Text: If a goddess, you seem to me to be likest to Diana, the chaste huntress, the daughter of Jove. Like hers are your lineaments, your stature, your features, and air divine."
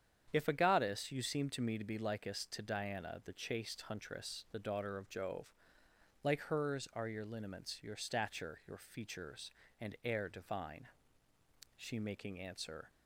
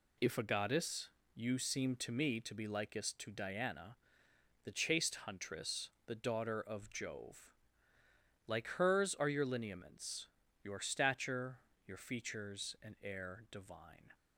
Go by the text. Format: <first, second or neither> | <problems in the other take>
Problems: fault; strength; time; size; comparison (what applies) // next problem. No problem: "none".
second | starts louder than the rest; strong; until 1.3 s; 8.5 dB // goes on to say "She making answer"; noticeable; from 11.7 s on; 1.1 s long